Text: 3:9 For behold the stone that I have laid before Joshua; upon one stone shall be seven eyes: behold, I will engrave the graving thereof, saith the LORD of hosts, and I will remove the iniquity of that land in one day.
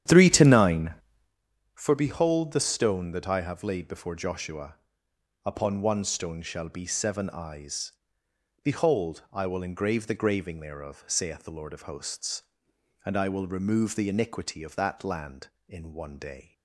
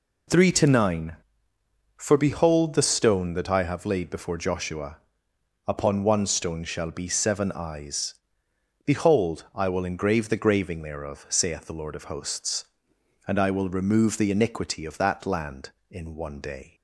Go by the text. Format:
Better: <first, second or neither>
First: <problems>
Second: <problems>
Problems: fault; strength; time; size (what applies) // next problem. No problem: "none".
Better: second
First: starts louder than the rest; strong; until 1.4 s; 10 dB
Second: none